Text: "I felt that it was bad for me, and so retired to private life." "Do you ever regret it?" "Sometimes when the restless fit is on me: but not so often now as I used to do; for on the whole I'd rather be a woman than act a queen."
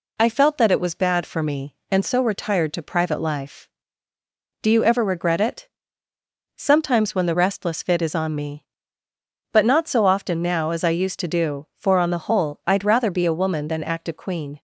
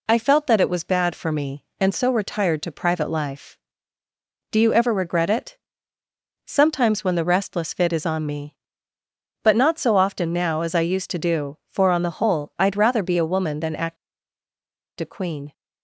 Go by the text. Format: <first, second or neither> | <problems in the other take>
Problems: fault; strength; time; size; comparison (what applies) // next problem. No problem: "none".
first | pauses between "act" and "a"; at 13.9 s; 1.0 s long